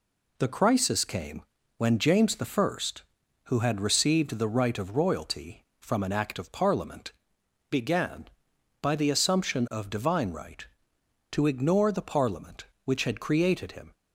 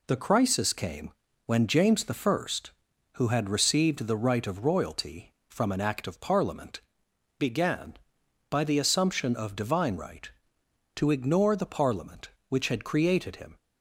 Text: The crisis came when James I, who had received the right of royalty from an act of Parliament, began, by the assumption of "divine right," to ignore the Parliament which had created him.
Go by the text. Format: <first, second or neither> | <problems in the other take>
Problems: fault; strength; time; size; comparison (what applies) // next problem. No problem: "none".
neither | pauses between "came" and "when"; slight; the same in both